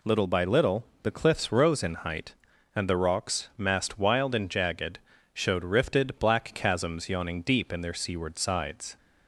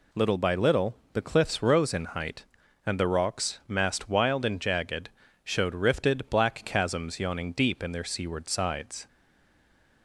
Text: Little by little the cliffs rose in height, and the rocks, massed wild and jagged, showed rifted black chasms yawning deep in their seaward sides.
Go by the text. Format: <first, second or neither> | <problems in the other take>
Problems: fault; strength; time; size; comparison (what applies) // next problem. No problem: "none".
first | pauses between "little" and "the"; slight; at 0.9 s; 0.18 s long; slight in the first // stays silent after the last word; from 9.0 s on; 1.0 s long